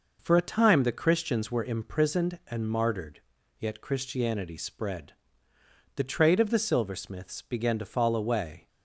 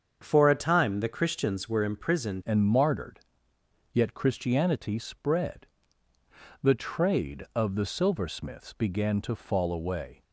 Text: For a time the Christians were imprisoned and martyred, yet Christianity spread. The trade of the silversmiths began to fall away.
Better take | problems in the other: first | starts louder than the rest; until 1.2 s; 7 dB // changes voice at "and"; from 2.4 s on; 7.8 s long

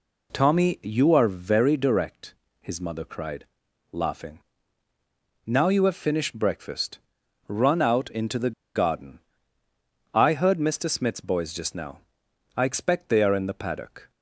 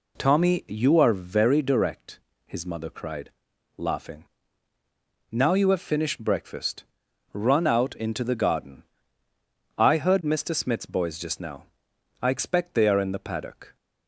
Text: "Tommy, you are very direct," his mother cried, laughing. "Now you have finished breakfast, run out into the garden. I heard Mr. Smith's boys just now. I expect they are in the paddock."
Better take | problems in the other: second | pauses between "the" and "garden"; slight; at 8.5 s; 0.24 s long

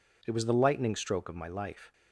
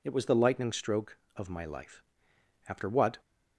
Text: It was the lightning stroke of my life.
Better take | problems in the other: first | goes on to say "After what"; from 2.6 s on; 0.50 s long

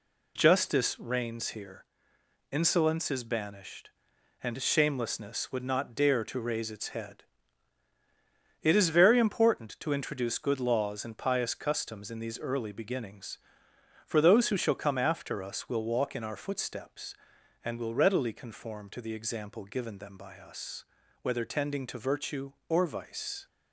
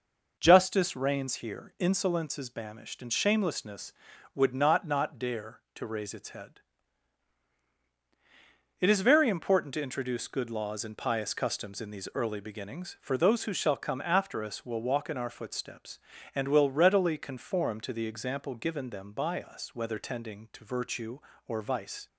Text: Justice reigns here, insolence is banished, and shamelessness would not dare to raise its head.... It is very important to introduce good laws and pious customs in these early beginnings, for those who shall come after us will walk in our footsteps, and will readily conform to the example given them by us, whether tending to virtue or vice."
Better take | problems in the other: first | says "not" twice; at 4.8 s

